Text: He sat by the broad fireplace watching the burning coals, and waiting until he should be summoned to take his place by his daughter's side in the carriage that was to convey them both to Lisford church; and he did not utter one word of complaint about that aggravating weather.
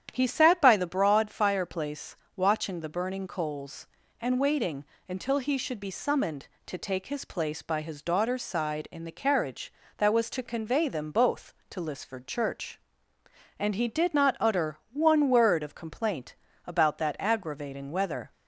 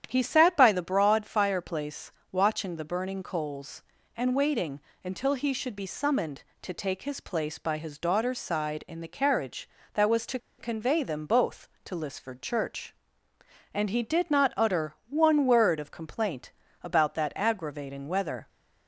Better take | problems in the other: first | starts louder than the rest; strong; until 1.0 s; 9.5 dB; strong in the first // pauses between "fireplace" and "watching"; slight; at 2.1 s; 0.20 s long; slight in the first // pauses between "waiting" and "until"; slight; at 4.7 s; 0.24 s long; slight in the first // pauses between "to" and "convey"; slight; at 10.3 s; 0.21 s long // pauses between "utter" and "one"; slight; at 14.9 s; 0.16 s long; slight in the first // pauses between "complaint" and "about"; slight; at 16.5 s; 0.30 s long; slight in the first

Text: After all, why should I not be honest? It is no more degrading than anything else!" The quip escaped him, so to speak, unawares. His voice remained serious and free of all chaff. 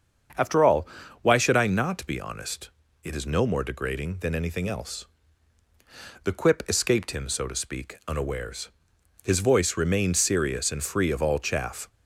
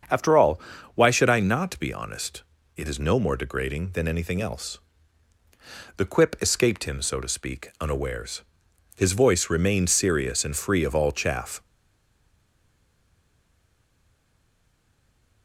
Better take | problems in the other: first | starts louder than the rest; until 1.4 s; 7 dB; also in the first // stays silent after the last word; strong; from 11.6 s on; 3.8 s long

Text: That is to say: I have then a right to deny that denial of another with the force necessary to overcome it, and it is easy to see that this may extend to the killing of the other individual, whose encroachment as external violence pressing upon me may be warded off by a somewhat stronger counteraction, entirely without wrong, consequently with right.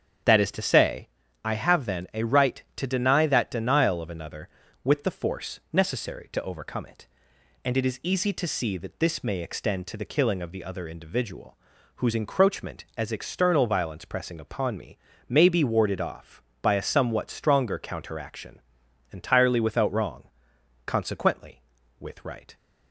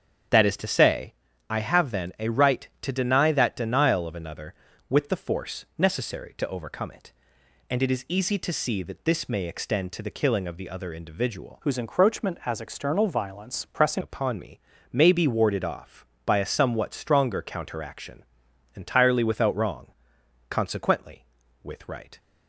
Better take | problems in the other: first | starts louder than the rest; strong; until 1.6 s; 8.5 dB; strong in the first // changes voice from "whose" to "pressing"; from 11.6 to 14.0 s; 2.4 s long // pauses between "me" and "may"; slight; at 14.5 s; 0.32 s long; slight in the first

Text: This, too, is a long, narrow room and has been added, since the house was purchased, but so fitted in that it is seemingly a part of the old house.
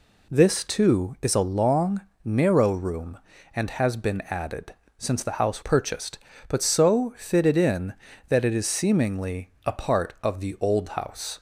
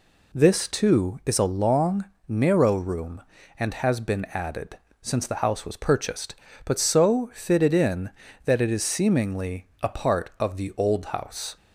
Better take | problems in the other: second | skips "was"; at 5.6 s // pauses between "seemingly" and "a"; slight; at 9.4 s; 0.16 s long; slight in the second

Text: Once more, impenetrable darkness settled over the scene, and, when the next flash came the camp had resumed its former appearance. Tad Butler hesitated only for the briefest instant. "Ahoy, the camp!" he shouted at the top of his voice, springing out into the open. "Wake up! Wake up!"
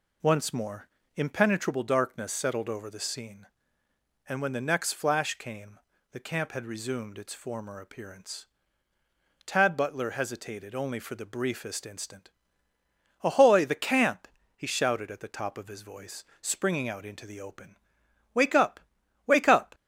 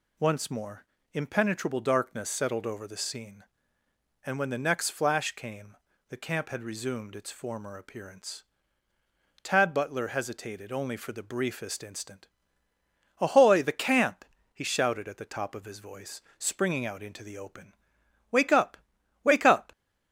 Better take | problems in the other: second | starts louder than the rest; slight; until 1.8 s; 3 dB // pauses between "came" and "the"; slight; at 5.7 s; 0.34 s long; slight in the second

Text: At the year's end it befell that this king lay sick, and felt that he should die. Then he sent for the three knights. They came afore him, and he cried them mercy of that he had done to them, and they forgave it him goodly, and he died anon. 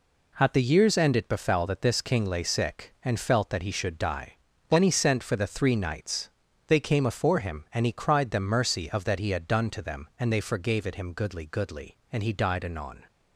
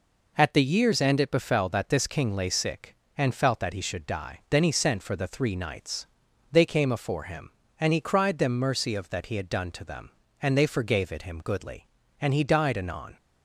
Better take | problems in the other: second | says "goodly" twice; at 11.4 s

